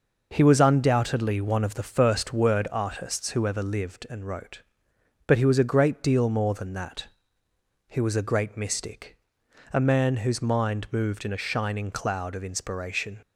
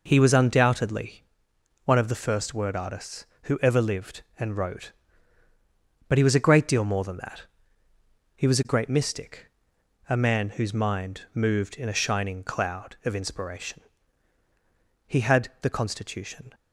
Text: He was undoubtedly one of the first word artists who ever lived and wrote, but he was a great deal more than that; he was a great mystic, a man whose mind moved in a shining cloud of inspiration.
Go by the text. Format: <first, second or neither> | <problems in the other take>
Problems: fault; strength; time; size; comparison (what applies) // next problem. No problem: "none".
first | pauses between "undoubtedly" and "one"; noticeable; at 1.2 s; 0.60 s long // goes on to say "He had the constitution"; from 15.0 s on; 1.4 s long